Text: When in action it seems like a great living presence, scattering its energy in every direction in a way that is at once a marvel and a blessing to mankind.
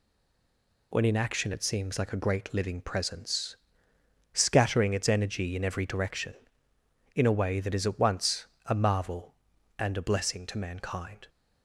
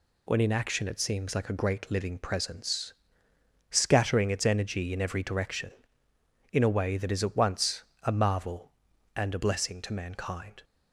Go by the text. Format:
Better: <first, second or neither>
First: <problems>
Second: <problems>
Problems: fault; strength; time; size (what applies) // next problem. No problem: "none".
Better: second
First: stays silent before the first word; slight; until 0.9 s; 0.9 s long // pauses between "once" and "a"; slight; at 8.4 s; 0.20 s long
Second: pauses between "once" and "a"; slight; at 7.8 s; 0.20 s long